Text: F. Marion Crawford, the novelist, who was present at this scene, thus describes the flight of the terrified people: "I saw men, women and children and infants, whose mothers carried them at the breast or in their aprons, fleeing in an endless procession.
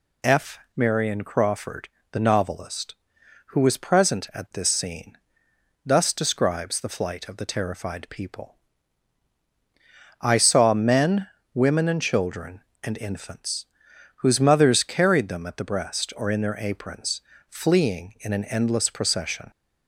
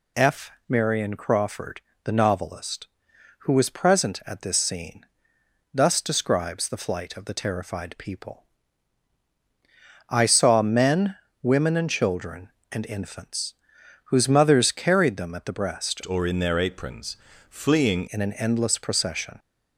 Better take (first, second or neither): first